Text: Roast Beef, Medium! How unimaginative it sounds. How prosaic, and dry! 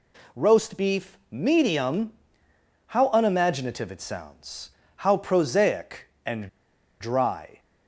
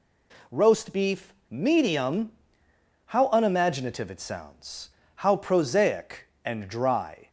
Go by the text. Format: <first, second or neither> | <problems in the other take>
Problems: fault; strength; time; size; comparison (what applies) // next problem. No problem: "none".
second | pauses between "and" and "dry"; noticeable; at 6.4 s; 0.51 s long